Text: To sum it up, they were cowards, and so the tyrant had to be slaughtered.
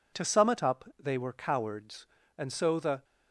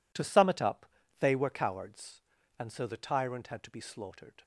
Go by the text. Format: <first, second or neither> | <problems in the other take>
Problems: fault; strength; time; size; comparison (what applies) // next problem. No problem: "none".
second | stops before "tyrant had to be slaughtered"; at 3.0 s